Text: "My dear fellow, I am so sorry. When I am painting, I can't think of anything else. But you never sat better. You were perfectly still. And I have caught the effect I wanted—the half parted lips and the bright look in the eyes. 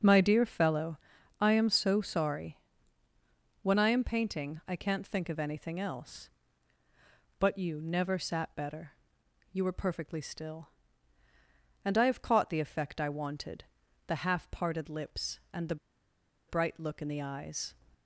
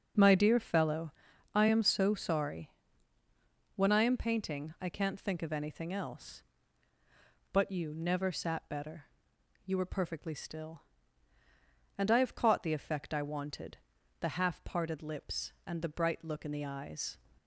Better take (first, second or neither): second